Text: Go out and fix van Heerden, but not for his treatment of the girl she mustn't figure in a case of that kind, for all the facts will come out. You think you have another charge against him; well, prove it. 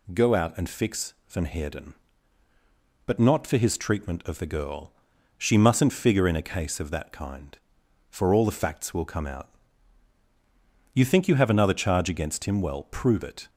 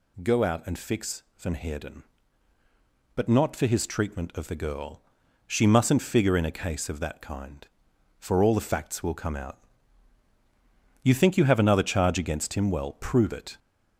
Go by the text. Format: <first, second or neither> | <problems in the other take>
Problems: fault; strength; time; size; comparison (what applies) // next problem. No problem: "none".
first | gets louder; noticeable; throughout; 5 dB // pauses between "girl" and "she"; at 5.0 s; 0.44 s long; also in the first